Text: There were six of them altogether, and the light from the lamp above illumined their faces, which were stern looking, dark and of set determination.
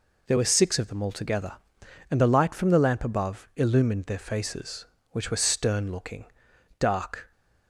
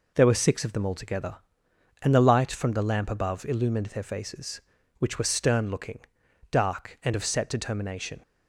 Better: second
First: stops before "and of set determination"; at 7.3 s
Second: none

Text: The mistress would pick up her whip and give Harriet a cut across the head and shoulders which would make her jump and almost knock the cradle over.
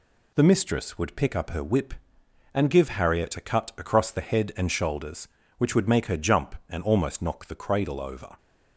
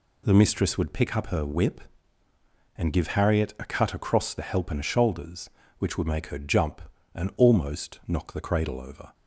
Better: first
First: none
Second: says "help" for "head"; at 4.4 s

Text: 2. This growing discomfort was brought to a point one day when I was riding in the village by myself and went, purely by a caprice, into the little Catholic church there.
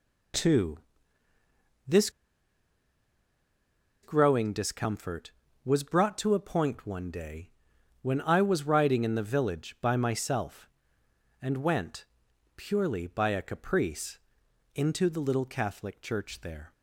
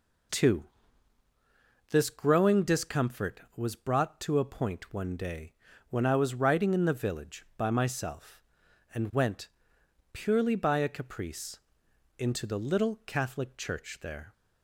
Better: second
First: pauses between "This" and "growing"; strong; at 2.0 s; 1.9 s long // pauses between "day" and "when"; noticeable; at 7.5 s; 0.50 s long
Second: pauses between "day" and "when"; at 5.5 s; 0.38 s long

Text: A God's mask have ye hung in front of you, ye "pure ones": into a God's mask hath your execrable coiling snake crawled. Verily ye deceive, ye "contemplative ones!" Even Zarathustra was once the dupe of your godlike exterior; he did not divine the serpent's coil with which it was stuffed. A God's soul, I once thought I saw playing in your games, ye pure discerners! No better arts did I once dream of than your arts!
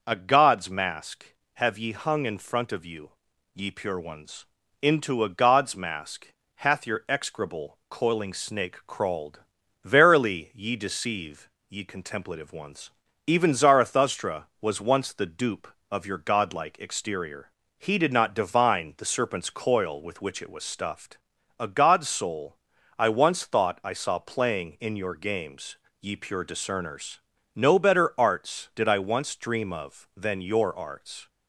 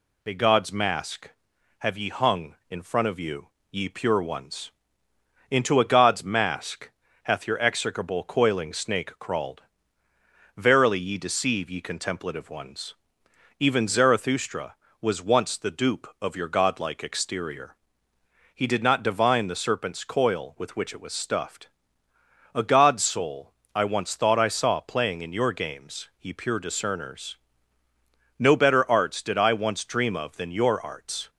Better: neither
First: pauses between "mask" and "hath"; slight; at 6.2 s; 0.30 s long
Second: pauses between "mask" and "hath"; slight; at 6.9 s; 0.32 s long

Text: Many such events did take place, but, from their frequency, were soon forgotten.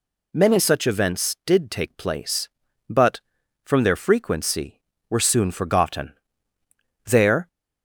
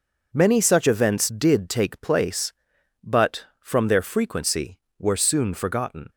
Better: second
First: goes on to say "There"; slight; from 7.0 s on; 0.42 s long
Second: none

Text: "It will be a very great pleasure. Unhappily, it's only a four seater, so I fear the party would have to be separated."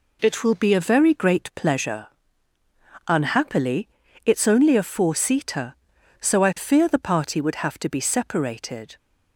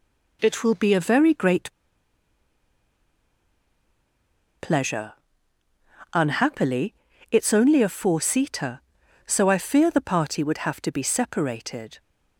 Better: first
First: none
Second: pauses between "great" and "pleasure"; strong; at 1.6 s; 2.9 s long

